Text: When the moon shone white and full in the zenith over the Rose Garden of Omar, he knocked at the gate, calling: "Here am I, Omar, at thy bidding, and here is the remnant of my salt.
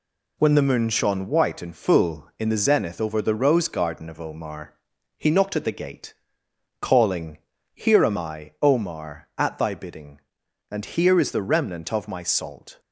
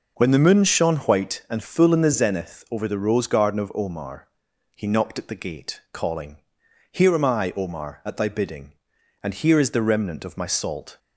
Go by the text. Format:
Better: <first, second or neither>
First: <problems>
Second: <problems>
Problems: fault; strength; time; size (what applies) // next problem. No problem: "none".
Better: neither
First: none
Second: none